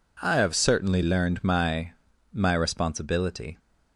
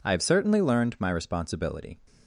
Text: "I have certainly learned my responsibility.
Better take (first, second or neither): second